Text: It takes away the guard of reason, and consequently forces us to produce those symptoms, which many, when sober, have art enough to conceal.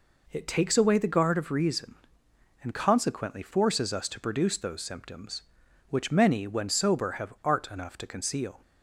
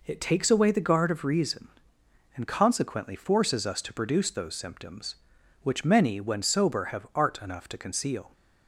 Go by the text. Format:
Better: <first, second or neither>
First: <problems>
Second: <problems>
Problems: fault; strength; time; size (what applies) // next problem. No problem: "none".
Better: neither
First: none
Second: none